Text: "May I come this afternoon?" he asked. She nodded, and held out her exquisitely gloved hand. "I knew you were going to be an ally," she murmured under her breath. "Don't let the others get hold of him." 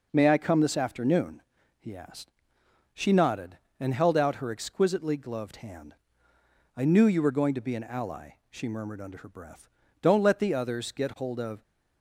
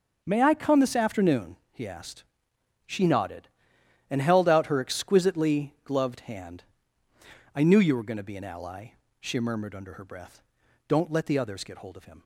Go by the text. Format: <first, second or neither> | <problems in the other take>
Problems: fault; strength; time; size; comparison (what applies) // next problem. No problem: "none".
second | stops before "him"; at 11.6 s